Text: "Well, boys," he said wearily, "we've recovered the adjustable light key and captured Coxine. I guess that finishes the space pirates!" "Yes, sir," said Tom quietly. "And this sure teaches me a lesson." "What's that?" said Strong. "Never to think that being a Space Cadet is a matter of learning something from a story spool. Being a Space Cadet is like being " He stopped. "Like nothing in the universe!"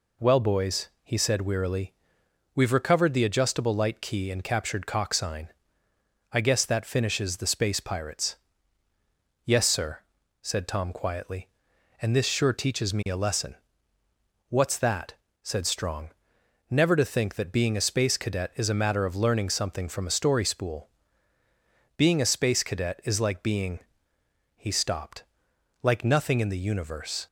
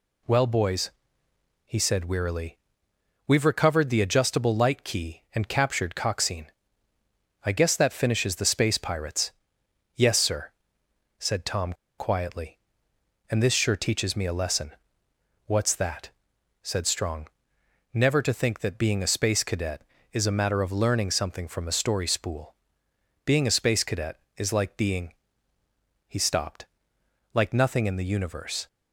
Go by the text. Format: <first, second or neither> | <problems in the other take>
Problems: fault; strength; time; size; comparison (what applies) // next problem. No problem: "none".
first | pauses between "Tom" and "quietly"; slight; at 11.7 s; 0.25 s long